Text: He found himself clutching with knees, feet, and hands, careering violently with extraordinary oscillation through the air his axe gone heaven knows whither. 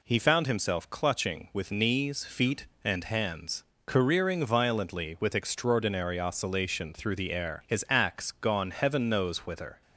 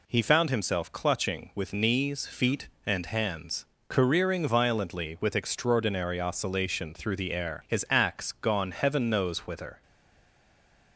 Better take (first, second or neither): first